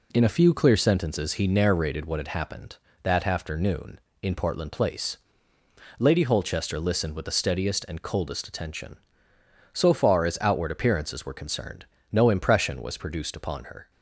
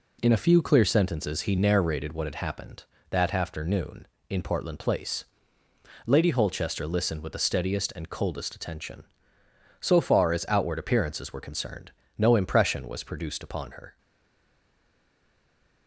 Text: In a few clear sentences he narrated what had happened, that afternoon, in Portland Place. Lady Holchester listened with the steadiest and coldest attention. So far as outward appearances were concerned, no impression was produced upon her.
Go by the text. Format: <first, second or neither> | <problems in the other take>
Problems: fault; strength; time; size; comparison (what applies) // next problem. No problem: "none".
first | stays silent after the last word; noticeable; from 13.9 s on; 1.9 s long